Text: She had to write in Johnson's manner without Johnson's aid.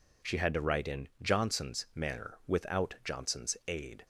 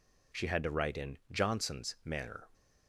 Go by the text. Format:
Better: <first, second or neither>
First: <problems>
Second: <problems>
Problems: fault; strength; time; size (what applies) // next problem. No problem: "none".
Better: first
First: none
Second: stops before "without Johnson's aid"; at 2.5 s